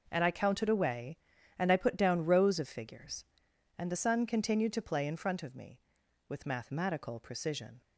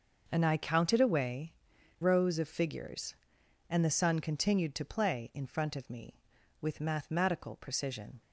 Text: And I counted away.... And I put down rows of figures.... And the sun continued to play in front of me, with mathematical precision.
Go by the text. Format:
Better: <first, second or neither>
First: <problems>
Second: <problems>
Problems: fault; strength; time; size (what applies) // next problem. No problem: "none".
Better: first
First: none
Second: starts louder than the rest; noticeable; until 1.3 s; 6 dB // skips "And I put down"; at 1.7 s